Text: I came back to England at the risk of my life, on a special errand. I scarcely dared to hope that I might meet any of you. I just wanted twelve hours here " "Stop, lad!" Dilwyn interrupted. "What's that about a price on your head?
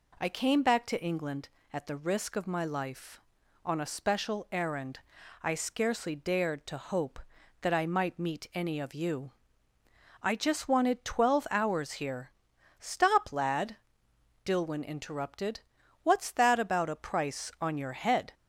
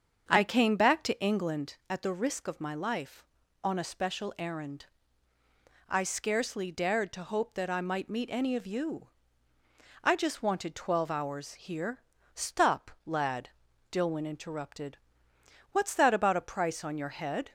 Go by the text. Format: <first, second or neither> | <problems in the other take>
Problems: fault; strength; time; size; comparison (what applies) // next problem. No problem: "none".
first | starts louder than the rest; strong; until 1.7 s; 7 dB